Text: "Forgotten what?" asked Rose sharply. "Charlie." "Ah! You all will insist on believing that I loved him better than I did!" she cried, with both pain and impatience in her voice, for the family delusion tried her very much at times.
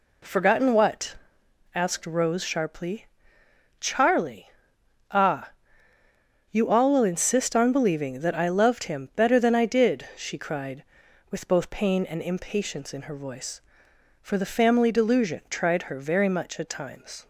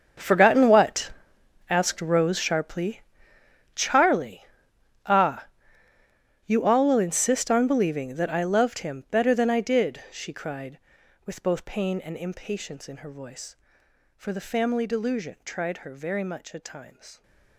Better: first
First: none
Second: gets quieter; strong; throughout; 16 dB

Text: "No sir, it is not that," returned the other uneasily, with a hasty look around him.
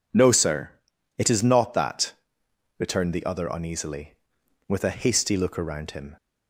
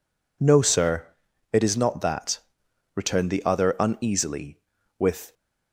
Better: first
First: none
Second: stops before "a hasty look around him"; at 5.3 s

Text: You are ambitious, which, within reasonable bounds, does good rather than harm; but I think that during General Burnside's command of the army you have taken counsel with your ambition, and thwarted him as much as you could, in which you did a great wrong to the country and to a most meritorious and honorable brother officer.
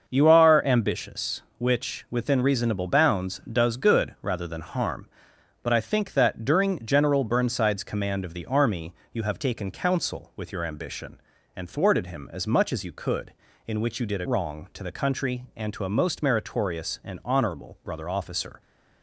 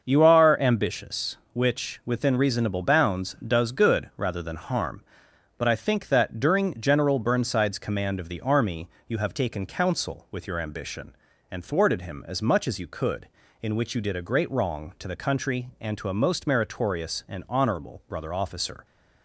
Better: second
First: starts louder than the rest; until 1.0 s; 6.5 dB // pauses between "army" and "you"; slight; at 8.9 s; 0.18 s long // skips "great"; at 14.2 s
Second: starts louder than the rest; until 1.0 s; 6.5 dB // pauses between "army" and "you"; slight; at 8.8 s; 0.18 s long

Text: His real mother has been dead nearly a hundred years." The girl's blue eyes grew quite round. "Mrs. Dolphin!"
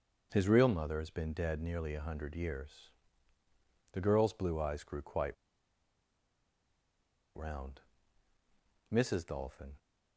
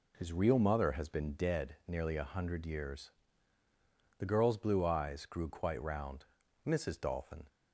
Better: second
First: starts louder than the rest; noticeable; until 1.3 s; 6 dB // pauses between "quite" and "round"; strong; at 5.3 s; 2.0 s long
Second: none

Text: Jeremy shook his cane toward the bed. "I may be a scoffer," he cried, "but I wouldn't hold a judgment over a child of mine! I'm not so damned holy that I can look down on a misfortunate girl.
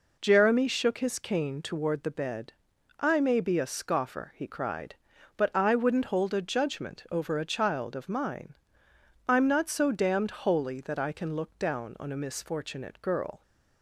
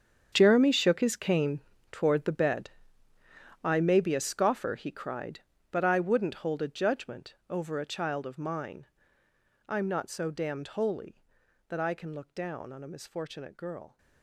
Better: first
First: none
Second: gets quieter; strong; throughout; 15.5 dB // pauses between "cane" and "toward"; slight; at 1.5 s; 0.32 s long // pauses between "judgment" and "over"; slight; at 7.3 s; 0.16 s long

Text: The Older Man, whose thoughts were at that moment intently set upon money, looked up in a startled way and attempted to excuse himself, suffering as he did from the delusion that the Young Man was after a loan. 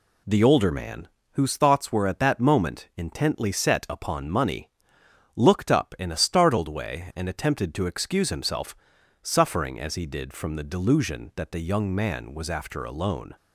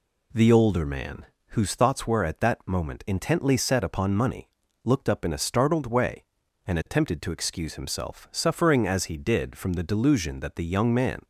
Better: first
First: none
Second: stops before "was after a loan"; at 11.2 s

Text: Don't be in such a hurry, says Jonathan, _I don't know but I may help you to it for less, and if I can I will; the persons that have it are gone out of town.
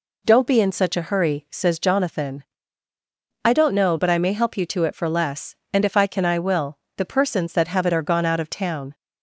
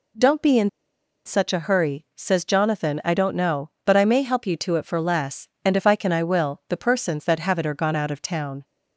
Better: first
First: none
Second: pauses between "in" and "such"; noticeable; at 0.6 s; 0.55 s long

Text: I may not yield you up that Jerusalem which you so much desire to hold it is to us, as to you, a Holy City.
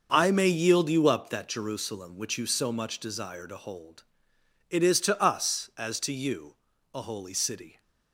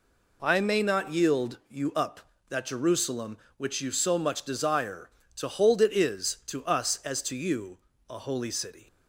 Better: second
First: starts louder than the rest; until 1.1 s; 6 dB // skips "not"; at 0.4 s // pauses between "hold" and "it"; noticeable; at 4.0 s; 0.66 s long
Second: none

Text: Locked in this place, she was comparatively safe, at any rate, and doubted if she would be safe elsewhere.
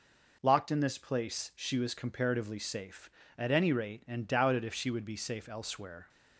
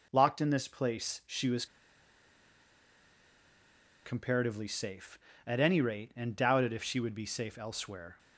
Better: first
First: none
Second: pauses between "was" and "comparatively"; strong; at 1.6 s; 2.3 s long

